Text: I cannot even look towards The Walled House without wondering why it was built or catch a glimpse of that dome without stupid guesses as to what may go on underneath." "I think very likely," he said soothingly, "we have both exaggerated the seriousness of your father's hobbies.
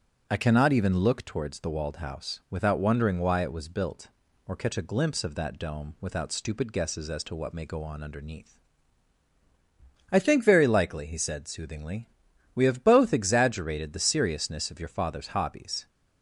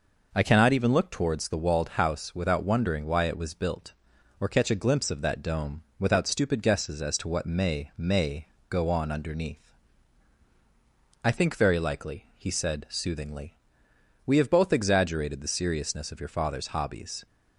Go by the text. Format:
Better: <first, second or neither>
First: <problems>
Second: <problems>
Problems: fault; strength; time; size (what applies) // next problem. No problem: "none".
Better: first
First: none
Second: pauses between "dome" and "without"; slight; at 5.8 s; 0.16 s long // says "may" twice; at 7.9 s